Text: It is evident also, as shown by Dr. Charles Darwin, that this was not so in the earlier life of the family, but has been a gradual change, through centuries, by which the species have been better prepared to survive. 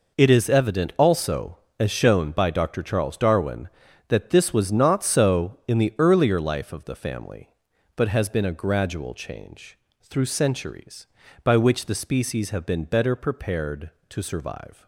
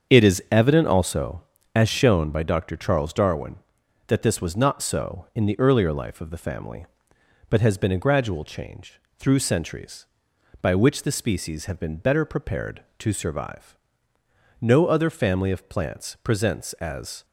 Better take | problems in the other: first | starts louder than the rest; strong; until 1.1 s; 7 dB // goes on to say "No other family of plants presents as"; strong; from 14.6 s on; 2.6 s long

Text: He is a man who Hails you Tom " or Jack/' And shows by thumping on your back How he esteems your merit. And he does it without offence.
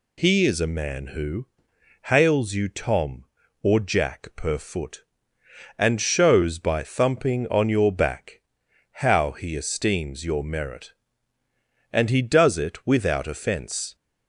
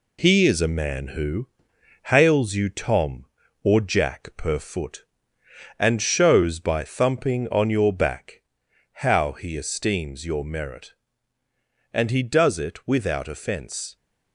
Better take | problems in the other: first | gets quieter; slight; throughout; 2.5 dB // pauses between "who" and "Hails"; noticeable; at 1.4 s; 0.66 s long; noticeable in the first // pauses between "back" and "How"; noticeable; at 8.4 s; 0.54 s long; noticeable in the first

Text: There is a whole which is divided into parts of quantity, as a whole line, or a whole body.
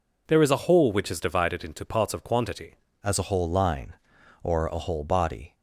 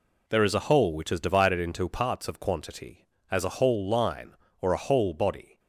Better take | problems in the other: second | changes voice at "as"; from 3.0 s on; 2.5 s long

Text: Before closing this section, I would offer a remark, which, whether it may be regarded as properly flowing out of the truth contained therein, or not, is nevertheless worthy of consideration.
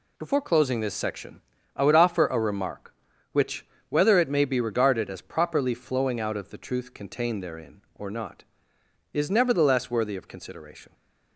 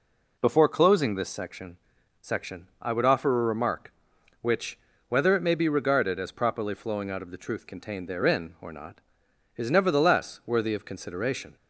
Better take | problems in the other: first | says "section" twice; at 2.2 s

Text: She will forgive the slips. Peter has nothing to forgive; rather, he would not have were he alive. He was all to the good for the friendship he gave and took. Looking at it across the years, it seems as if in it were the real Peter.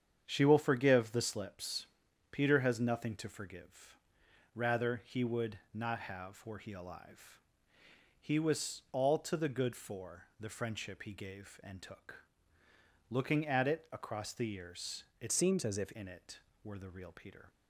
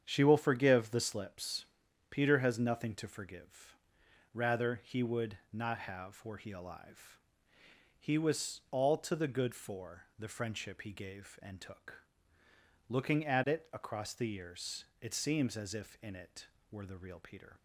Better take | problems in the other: second | starts louder than the rest; strong; until 1.2 s; 8 dB; strong in the second // pauses between "for" and "the"; slight; at 10.2 s; 0.16 s long; slight in the second // changes voice from "seems" to "if"; from 15.3 to 15.9 s; 0.6 s long

